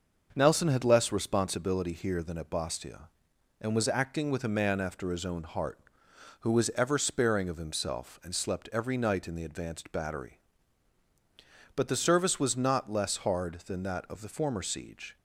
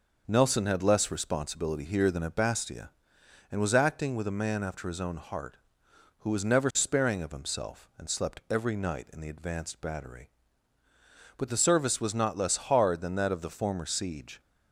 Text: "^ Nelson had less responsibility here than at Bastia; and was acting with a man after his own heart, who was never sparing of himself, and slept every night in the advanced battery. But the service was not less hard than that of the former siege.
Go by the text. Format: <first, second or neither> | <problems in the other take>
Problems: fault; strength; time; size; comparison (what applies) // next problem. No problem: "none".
second | starts louder than the rest; noticeable; until 1.3 s; 6 dB // says "ever" for "never"; at 6.7 s